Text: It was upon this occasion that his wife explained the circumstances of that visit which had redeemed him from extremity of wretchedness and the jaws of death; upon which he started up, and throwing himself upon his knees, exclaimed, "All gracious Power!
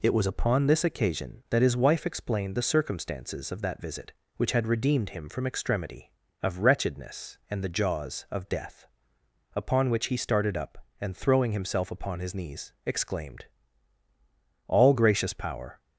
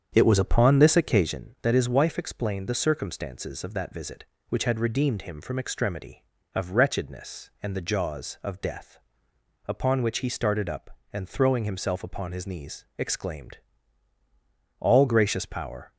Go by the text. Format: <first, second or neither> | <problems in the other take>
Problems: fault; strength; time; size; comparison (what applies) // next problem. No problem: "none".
first | starts louder than the rest; strong; until 1.4 s; 8 dB